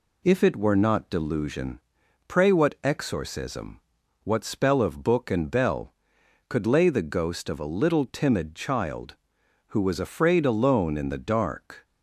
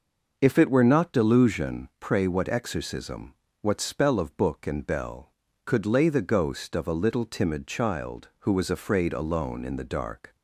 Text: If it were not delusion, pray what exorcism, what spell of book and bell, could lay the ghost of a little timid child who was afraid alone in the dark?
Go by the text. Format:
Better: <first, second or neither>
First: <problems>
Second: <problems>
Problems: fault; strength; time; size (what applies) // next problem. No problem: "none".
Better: neither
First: none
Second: none